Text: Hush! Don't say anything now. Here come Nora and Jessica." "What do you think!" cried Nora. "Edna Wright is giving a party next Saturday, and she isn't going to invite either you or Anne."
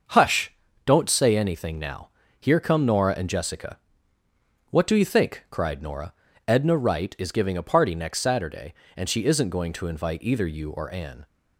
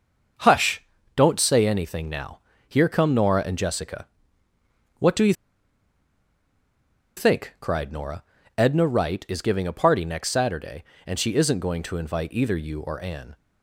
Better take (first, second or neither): first